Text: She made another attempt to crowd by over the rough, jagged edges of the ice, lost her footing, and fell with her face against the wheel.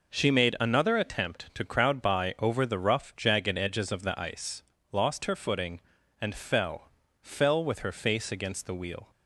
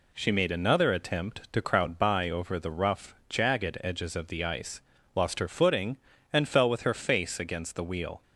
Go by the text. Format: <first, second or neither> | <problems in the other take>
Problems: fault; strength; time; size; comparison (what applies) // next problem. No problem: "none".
second | says "fell" twice; at 7.2 s